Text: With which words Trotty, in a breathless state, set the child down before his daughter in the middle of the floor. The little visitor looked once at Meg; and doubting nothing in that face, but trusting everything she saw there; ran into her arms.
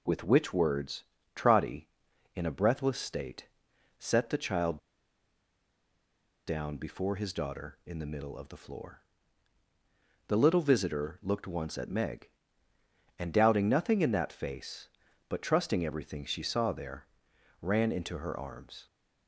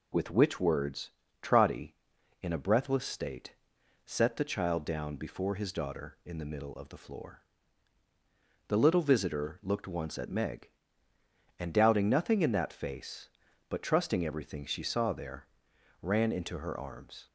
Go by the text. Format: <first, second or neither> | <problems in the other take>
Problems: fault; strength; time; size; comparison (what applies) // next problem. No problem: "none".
second | pauses between "words" and "Trotty"; slight; at 1.0 s; 0.32 s long; slight in the second // pauses between "child" and "down"; strong; at 4.7 s; 1.6 s long